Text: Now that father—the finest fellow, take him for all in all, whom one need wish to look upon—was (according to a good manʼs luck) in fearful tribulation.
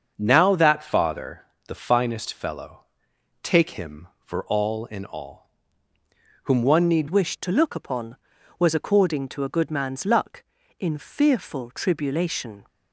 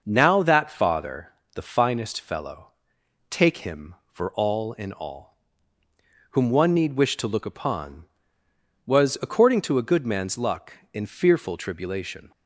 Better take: second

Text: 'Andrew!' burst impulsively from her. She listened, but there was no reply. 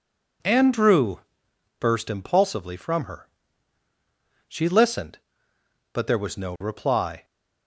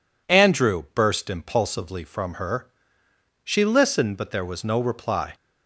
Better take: neither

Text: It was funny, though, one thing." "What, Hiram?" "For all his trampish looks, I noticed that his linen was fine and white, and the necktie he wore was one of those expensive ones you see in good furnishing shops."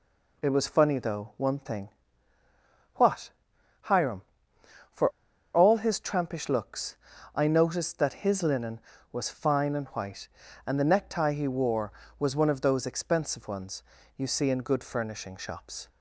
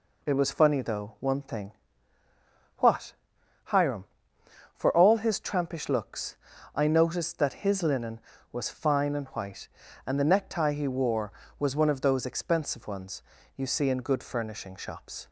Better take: second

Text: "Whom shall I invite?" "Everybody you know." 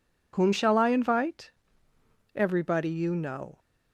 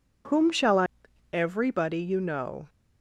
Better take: first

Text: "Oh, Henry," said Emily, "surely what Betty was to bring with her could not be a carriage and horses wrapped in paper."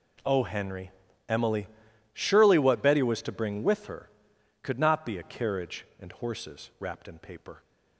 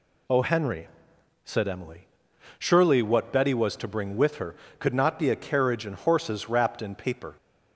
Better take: second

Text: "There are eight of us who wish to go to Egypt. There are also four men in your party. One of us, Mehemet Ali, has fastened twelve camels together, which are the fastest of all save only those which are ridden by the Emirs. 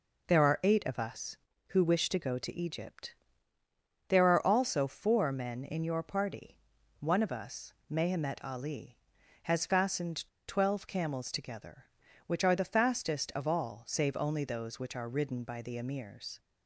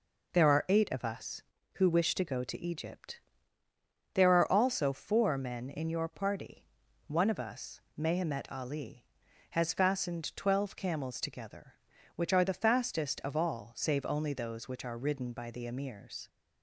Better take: second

